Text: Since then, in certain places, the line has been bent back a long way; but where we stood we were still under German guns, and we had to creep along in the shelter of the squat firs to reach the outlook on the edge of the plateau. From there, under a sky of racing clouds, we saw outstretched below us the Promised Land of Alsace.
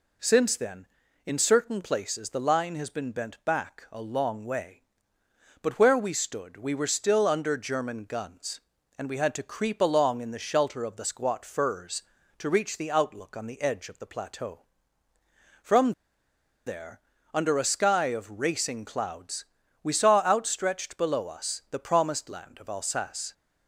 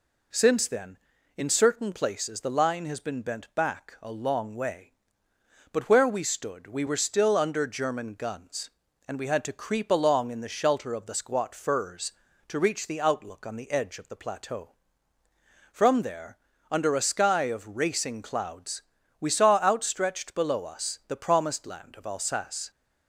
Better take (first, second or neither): second